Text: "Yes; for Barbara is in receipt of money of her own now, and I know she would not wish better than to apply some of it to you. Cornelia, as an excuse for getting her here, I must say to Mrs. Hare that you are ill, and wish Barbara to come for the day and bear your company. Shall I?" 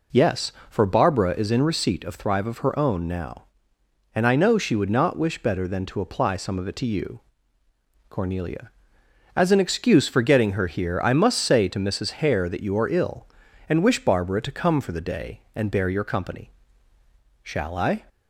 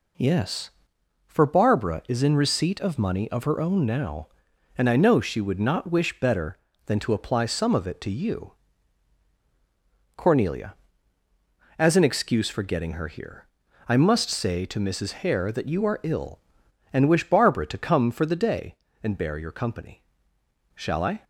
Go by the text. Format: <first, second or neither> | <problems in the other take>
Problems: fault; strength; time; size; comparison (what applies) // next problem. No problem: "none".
second | says "thrive" for "money"; at 2.1 s